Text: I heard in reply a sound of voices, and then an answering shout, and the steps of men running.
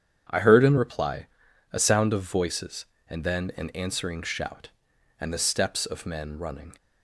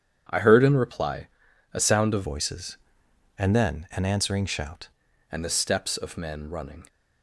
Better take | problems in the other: first | starts louder than the rest; strong; until 1.7 s; 8.5 dB; strong in the first // pauses between "reply" and "a"; noticeable; at 1.2 s; 0.46 s long; noticeable in the first // changes voice from "voices" to "shout"; from 2.2 to 4.8 s; 2.6 s long

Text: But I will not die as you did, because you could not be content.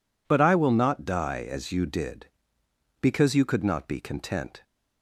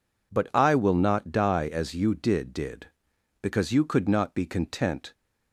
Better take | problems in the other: first | says "did" twice; at 2.5 s

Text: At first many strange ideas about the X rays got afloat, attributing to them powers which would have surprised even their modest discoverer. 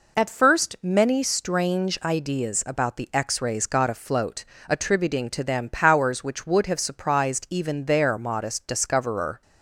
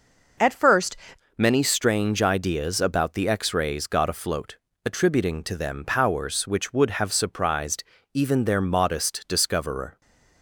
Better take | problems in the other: first | changes voice at "many"; from 1.3 s on; 8.7 s long // pauses between "surprised" and "even"; slight; at 7.8 s; 0.30 s long // stays silent after the last word; slight; from 9.9 s on; 0.5 s long

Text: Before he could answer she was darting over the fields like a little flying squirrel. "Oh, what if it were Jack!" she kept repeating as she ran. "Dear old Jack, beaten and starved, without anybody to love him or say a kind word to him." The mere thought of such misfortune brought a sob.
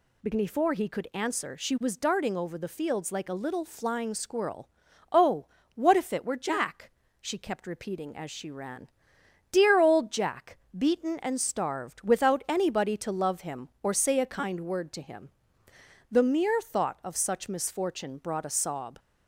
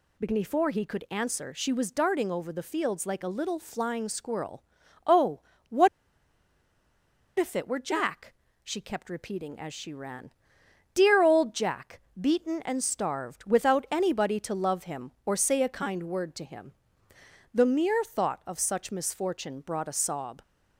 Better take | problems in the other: first | pauses between "what" and "if"; strong; at 5.8 s; 1.4 s long

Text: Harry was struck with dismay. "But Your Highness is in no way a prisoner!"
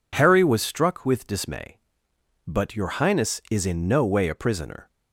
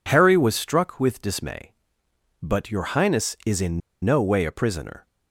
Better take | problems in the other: first | pauses between "in" and "no"; slight; at 3.8 s; 0.24 s long

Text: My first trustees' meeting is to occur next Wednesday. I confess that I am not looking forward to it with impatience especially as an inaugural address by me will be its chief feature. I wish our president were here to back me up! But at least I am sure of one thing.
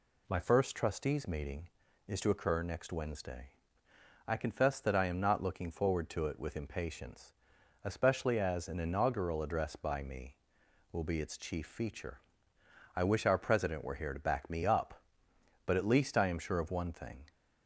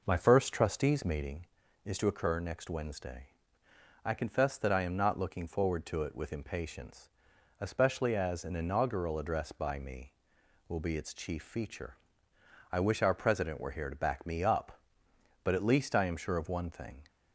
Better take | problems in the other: first | starts louder than the rest; noticeable; until 1.3 s; 5 dB // pauses between "impatience" and "especially"; noticeable; at 7.0 s; 0.54 s long; noticeable in the first

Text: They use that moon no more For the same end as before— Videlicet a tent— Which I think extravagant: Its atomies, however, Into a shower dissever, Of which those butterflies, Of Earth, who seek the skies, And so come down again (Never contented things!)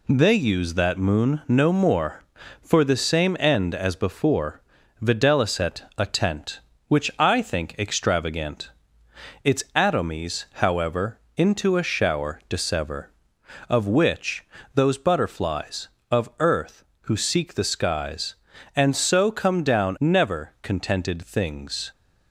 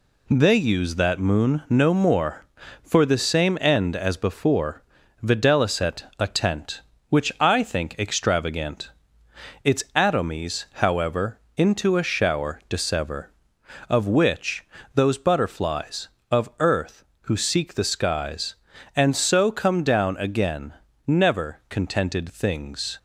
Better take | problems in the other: second | pauses between "Videlicet" and "a"; slight; at 5.8 s; 0.16 s long; slight in the second // pauses between "which" and "those"; slight; at 14.4 s; 0.32 s long; slight in the second // skips "again"; at 19.9 s

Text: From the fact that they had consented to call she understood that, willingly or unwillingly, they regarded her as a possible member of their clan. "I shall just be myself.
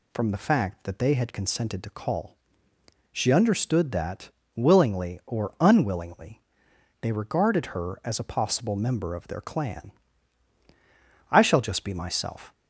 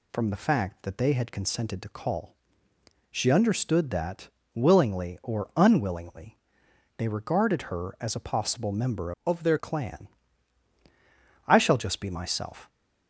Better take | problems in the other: first | pauses between "call" and "she"; noticeable; at 2.3 s; 0.78 s long; noticeable in the first // changes voice from "of" to "their"; from 9.2 to 9.5 s; 0.3 s long

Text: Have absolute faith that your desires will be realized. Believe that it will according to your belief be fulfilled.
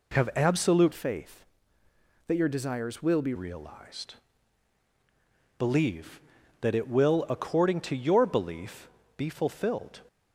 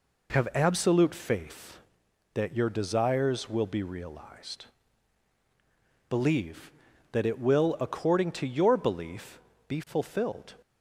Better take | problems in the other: second | changes voice from "faith" to "be"; from 0.9 to 3.3 s; 2.4 s long // pauses between "belief" and "be"; slight; at 8.8 s; 0.28 s long; slight in the second

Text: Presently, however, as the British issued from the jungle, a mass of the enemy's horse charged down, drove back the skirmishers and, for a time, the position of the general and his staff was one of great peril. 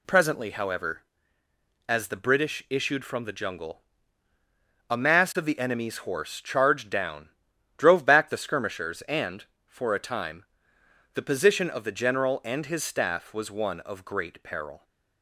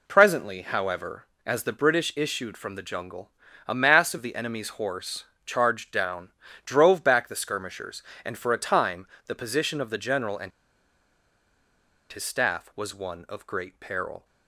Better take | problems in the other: first | pauses between "horse" and "charged"; slight; at 5.2 s; 0.22 s long // pauses between "and" and "his"; strong; at 10.5 s; 1.6 s long

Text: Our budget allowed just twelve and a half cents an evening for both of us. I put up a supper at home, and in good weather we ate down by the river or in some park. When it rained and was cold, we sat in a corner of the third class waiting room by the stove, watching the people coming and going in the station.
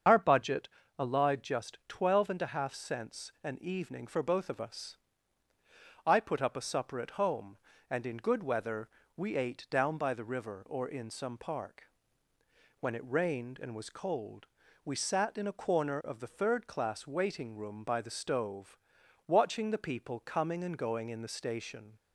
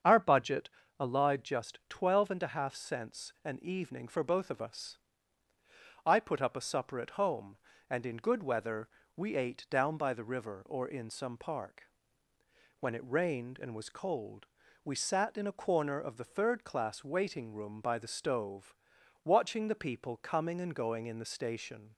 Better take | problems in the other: second | loses the start of "Our"; at 0.0 s; 35 ms // starts louder than the rest; strong; until 1.3 s; 7 dB; strong in the second // pauses between "budget" and "allowed"; slight; at 0.6 s; 0.28 s long; slight in the second // pauses between "weather" and "we"; slight; at 8.8 s; 0.30 s long; slight in the second

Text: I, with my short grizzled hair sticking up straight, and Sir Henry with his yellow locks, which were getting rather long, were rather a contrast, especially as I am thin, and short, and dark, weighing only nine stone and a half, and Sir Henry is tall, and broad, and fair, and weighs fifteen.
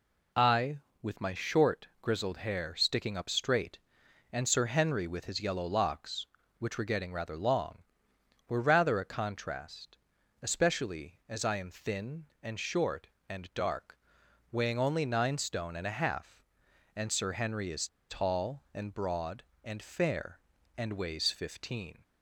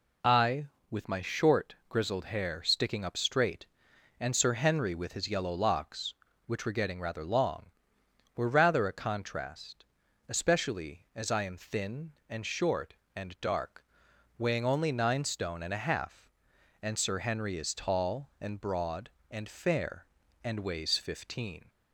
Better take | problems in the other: second | pauses between "is" and "tall"; slight; at 17.8 s; 0.21 s long

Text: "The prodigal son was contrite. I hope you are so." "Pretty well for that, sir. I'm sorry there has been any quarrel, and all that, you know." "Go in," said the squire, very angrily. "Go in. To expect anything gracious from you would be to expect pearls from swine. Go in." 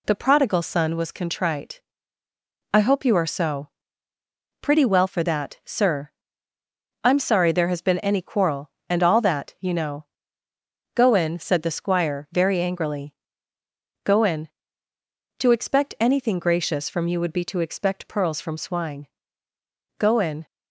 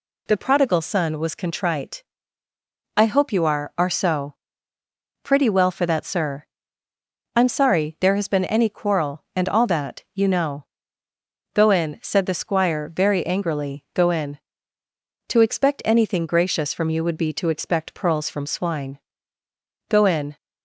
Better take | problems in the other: first | says "are" twice; at 3.7 s

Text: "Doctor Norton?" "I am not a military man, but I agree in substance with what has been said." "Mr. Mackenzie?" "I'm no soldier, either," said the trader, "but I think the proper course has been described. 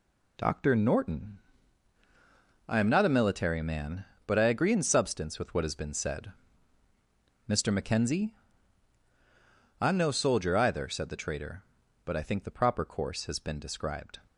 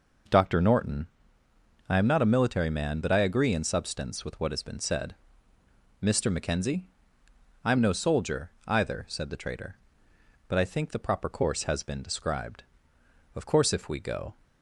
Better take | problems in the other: first | goes on to say "Of course if we go"; noticeable; from 13.3 s on; 1.0 s long

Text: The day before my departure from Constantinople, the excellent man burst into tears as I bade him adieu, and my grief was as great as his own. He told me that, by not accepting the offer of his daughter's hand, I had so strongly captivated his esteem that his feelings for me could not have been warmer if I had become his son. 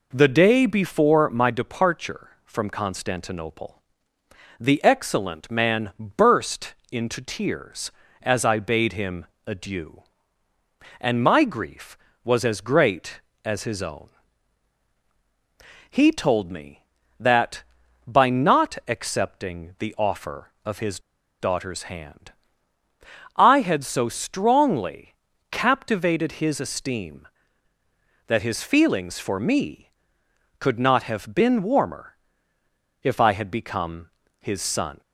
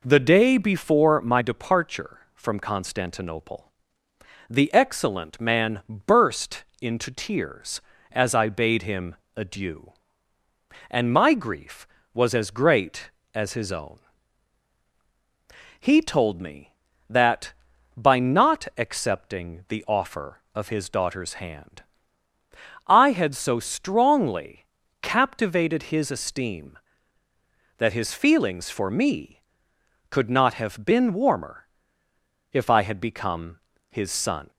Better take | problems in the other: second | pauses between "burst" and "into"; slight; at 6.7 s; 0.18 s long; slight in the second // pauses between "him" and "adieu"; slight; at 9.2 s; 0.22 s long; slight in the second // pauses between "his" and "daughter's"; at 20.9 s; 0.40 s long // pauses between "strongly" and "captivated"; at 25.1 s; 0.38 s long; also in the second // pauses between "warmer" and "if"; noticeable; at 32.1 s; 0.86 s long; noticeable in the second // pauses between "become" and "his"; slight; at 34.1 s; 0.32 s long; slight in the second

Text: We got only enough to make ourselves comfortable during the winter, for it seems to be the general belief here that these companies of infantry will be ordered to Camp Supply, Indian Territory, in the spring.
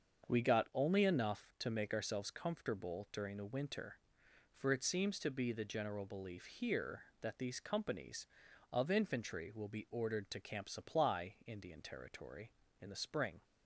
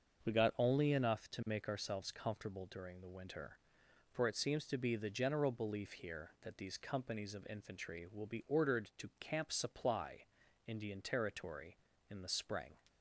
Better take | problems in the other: neither | starts louder than the rest; the same in both

